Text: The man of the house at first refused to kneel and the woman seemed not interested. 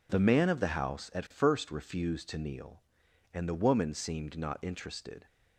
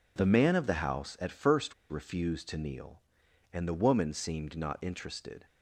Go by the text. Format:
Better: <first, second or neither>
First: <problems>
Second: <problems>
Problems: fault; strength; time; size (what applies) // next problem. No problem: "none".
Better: first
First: none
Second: pauses between "first" and "refused"; slight; at 1.7 s; 0.17 s long